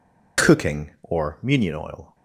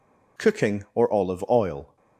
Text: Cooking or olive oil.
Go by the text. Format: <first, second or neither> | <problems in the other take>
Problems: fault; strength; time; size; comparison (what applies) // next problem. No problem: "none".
second | says "munion" for "olive"; at 1.4 s